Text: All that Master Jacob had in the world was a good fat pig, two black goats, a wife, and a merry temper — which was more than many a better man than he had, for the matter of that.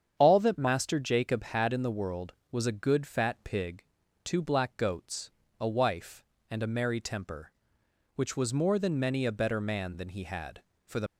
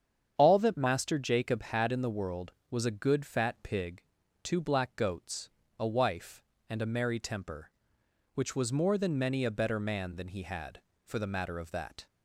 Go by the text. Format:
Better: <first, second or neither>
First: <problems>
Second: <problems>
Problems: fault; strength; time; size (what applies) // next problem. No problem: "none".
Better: second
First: starts louder than the rest; strong; until 1.2 s; 8 dB // stops before "matter of that"; at 11.0 s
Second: starts louder than the rest; strong; until 1.4 s; 8 dB